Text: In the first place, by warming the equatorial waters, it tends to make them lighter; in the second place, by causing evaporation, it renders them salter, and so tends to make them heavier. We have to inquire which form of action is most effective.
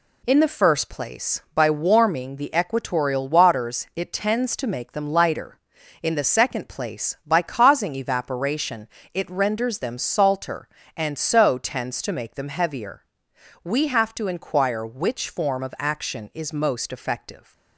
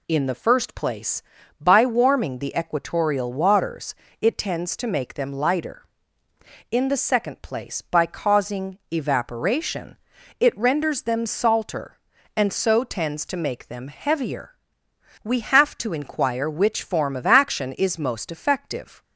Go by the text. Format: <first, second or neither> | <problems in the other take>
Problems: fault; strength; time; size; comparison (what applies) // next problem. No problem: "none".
neither | none